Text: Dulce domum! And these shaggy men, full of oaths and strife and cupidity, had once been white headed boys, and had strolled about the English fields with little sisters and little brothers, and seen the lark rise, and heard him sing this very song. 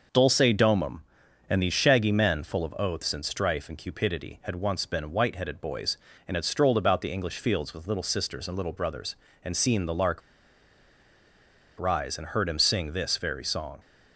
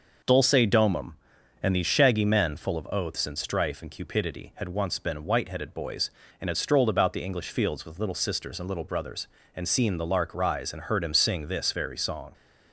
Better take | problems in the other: second | pauses between "lark" and "rise"; strong; at 10.2 s; 1.5 s long

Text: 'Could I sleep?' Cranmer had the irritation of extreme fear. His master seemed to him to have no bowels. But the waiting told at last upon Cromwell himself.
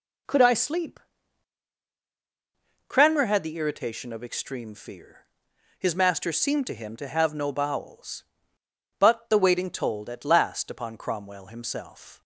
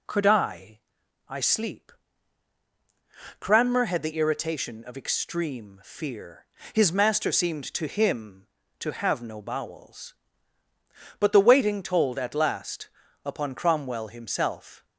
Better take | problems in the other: first | says "I" twice; at 1.2 s // pauses between "last" and "upon"; at 12.8 s; 0.38 s long

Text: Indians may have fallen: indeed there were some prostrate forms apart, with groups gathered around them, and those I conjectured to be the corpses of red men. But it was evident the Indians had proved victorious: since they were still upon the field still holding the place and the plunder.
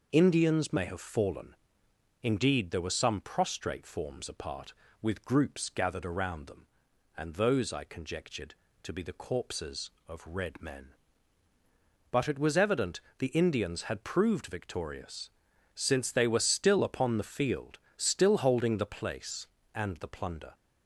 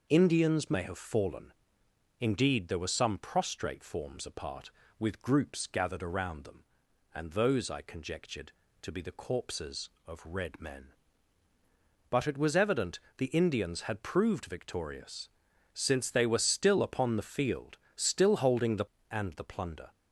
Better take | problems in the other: first | pauses between "evident" and "the"; slight; at 12.9 s; 0.18 s long; slight in the first // pauses between "field" and "still"; slight; at 17.7 s; 0.20 s long; slight in the first // skips "place"; at 18.9 s

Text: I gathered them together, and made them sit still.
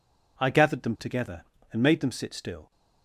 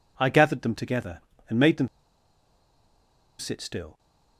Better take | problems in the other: first | pauses between "them" and "sit"; strong; at 1.8 s; 1.5 s long

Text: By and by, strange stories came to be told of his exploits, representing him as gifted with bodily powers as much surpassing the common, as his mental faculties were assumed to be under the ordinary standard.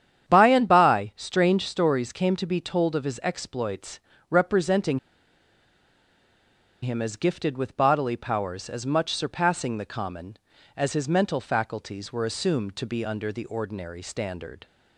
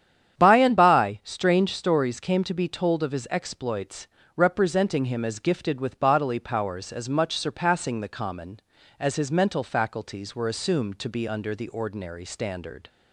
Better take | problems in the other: second | starts louder than the rest; strong; until 1.3 s; 9.5 dB; strong in the second // pauses between "representing" and "him"; strong; at 4.9 s; 1.8 s long

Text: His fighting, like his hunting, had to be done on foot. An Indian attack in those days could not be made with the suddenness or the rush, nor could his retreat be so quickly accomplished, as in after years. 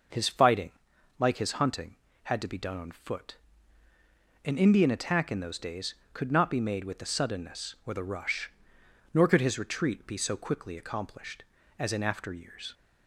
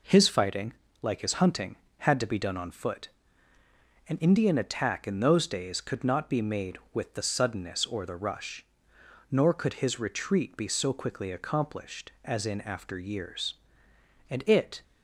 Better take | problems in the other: first | goes on to say "And it"; from 14.2 s on; 0.54 s long

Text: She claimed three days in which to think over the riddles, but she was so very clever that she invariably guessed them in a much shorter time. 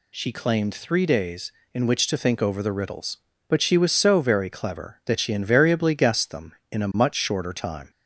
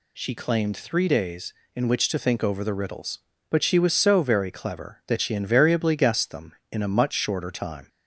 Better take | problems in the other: neither | none

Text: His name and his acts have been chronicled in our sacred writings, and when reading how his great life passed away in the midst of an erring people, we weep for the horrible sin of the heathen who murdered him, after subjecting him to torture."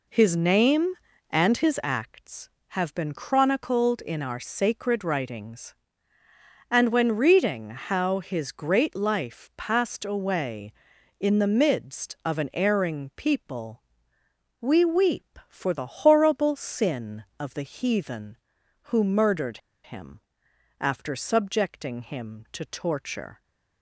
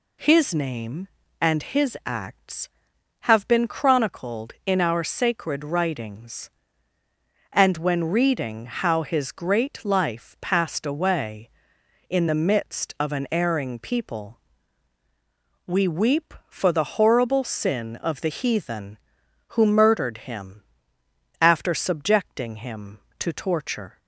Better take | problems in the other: second | pauses between "murdered" and "him"; slight; at 19.5 s; 0.25 s long

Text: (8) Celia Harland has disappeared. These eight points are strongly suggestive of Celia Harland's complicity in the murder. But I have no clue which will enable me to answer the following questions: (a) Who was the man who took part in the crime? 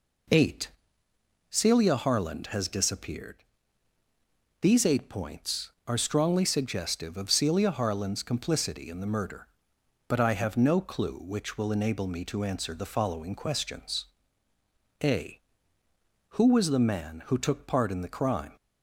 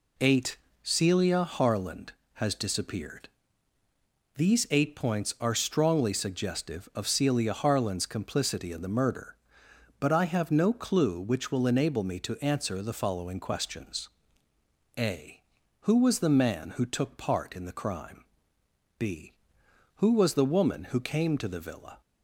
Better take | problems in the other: first | goes on to say "b Who was the woman who came to the villa"; strong; from 18.9 s on; 3.0 s long

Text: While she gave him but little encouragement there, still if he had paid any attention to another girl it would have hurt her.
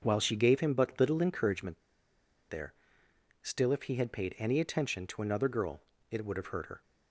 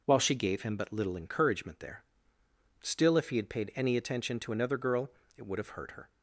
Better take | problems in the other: second | starts louder than the rest; until 1.0 s; 6.5 dB // pauses between "encouragement" and "there"; noticeable; at 1.8 s; 0.68 s long // pauses between "girl" and "it"; slight; at 5.8 s; 0.28 s long; slight in the second

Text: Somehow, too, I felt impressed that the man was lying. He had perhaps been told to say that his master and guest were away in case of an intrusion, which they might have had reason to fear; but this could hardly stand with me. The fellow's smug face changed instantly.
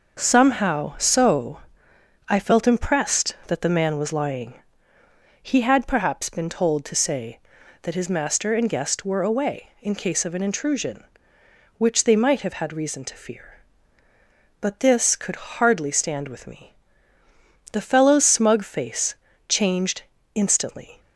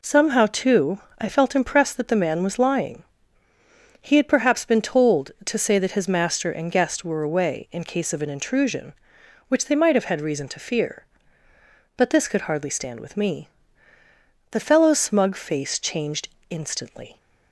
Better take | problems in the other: second | says "so" for "too"; at 0.9 s // pauses between "face" and "changed"; slight; at 19.1 s; 0.34 s long // pauses between "changed" and "instantly"; slight; at 20.0 s; 0.32 s long; slight in the second

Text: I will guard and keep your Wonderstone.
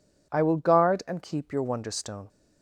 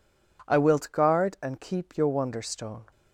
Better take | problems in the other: first | says "wilt" for "will"; at 0.5 s

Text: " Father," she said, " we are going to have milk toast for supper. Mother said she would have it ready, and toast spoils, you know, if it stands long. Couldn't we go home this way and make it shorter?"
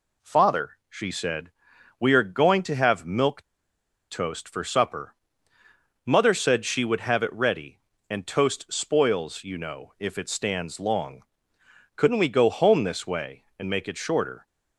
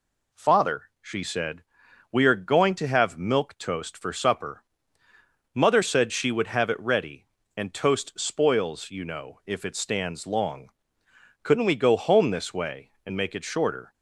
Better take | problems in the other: second | pauses between "milk" and "toast"; noticeable; at 3.4 s; 0.65 s long

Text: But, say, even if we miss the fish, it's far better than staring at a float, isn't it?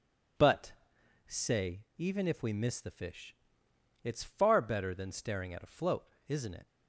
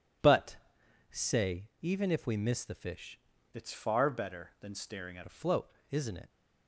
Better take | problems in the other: first | changes voice from "it's" to "at"; from 3.5 to 5.2 s; 1.7 s long

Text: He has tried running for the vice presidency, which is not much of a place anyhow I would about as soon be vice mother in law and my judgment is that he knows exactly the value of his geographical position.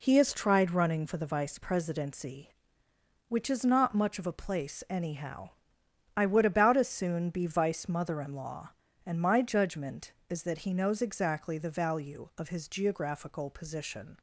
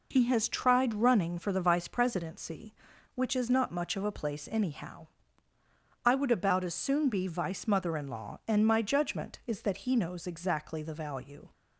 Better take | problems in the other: first | pauses between "anyhow" and "I"; noticeable; at 5.0 s; 0.96 s long; noticeable in the first // stops before "of his geographical position"; at 11.5 s

